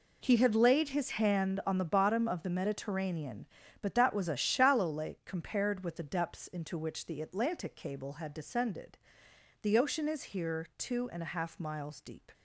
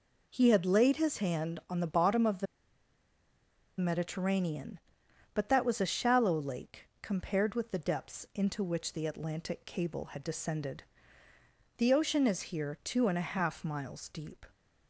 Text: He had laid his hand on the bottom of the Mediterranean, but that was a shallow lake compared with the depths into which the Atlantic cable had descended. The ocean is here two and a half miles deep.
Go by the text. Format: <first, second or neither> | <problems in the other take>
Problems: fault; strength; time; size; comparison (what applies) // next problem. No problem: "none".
first | pauses between "the" and "Mediterranean"; strong; at 2.4 s; 1.3 s long // pauses between "lake" and "compared"; slight; at 6.8 s; 0.16 s long